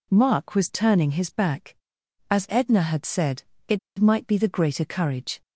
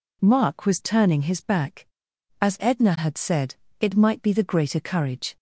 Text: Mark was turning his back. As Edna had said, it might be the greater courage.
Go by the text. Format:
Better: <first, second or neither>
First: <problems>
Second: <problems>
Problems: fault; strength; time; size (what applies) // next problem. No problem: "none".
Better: second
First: pauses between "it" and "might"; slight; at 3.7 s; 0.19 s long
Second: none